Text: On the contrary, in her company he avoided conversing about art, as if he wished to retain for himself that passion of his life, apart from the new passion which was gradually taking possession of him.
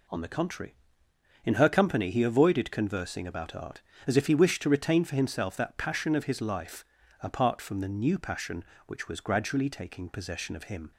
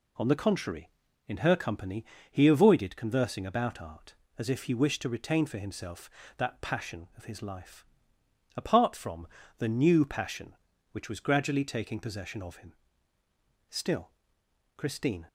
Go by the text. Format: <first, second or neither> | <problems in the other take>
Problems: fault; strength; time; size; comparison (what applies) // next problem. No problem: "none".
first | pauses between "company" and "he"; slight; at 2.0 s; 0.24 s long // pauses between "from" and "the"; slight; at 9.2 s; 0.30 s long // goes on to say "Still Christine"; from 13.6 s on; 1.5 s long